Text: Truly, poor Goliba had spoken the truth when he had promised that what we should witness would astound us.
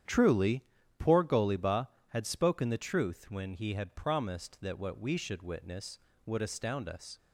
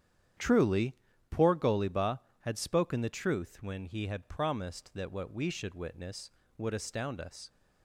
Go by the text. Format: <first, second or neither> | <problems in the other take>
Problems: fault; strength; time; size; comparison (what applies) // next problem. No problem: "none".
neither | starts louder than the rest; strong; the same in both